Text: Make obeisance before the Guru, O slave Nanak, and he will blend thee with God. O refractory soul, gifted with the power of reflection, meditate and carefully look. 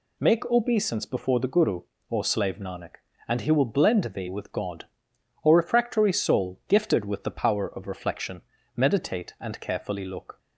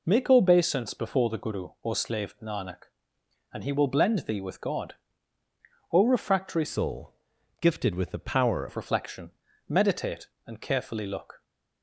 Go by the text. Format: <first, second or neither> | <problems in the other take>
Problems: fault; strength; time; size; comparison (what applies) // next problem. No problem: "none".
first | changes voice from "soul" to "power"; from 6.6 to 8.6 s; 2.0 s long